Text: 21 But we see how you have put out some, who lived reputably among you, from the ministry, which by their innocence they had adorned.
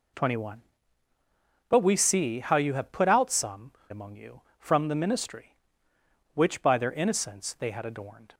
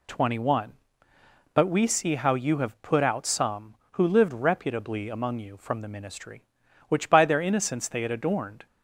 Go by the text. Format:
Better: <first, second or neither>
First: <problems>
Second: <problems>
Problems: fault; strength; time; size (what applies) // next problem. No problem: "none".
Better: second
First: skips "who lived reputably"; at 3.8 s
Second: none